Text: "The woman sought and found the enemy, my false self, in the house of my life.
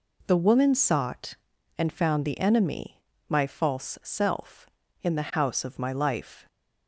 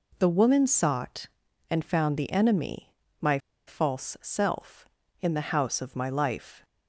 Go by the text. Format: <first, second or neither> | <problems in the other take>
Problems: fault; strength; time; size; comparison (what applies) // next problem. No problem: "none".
first | pauses between "my" and "false"; slight; at 3.3 s; 0.27 s long